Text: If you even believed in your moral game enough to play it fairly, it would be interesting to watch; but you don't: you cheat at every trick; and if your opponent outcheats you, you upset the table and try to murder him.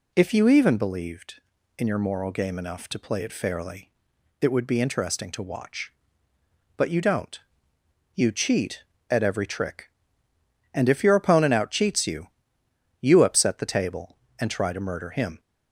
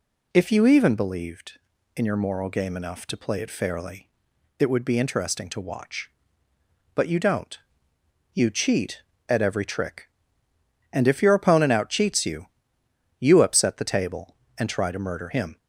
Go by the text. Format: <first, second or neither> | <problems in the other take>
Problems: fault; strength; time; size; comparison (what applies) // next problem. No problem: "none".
neither | none